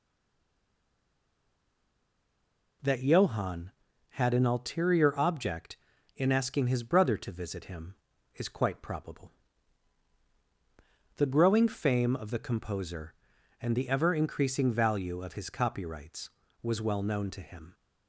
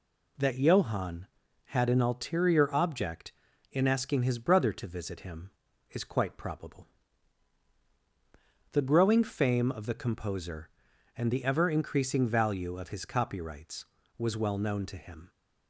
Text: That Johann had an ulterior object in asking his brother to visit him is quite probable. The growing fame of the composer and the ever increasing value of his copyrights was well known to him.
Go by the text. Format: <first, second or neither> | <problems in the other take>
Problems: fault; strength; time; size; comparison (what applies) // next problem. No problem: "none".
second | stays silent before the first word; strong; until 2.8 s; 2.8 s long